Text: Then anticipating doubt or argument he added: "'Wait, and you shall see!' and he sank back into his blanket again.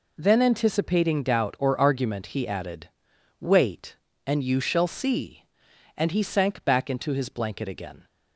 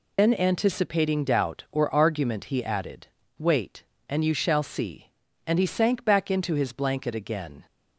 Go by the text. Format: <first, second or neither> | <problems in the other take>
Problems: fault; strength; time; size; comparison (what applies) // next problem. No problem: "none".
first | loses the start of "Then"; at 0.1 s; 90 ms